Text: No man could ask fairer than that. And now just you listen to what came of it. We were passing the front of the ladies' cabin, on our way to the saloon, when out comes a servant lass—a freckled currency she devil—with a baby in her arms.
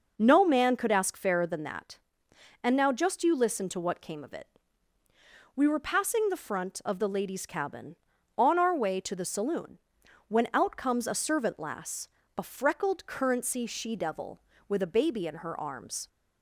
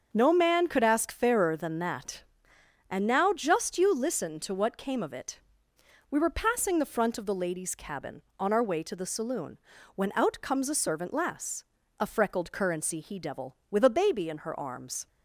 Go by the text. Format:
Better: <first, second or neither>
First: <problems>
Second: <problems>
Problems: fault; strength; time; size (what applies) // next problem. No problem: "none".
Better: first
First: none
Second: starts louder than the rest; until 1.1 s; 6.5 dB // says "he" for "she"; at 13.0 s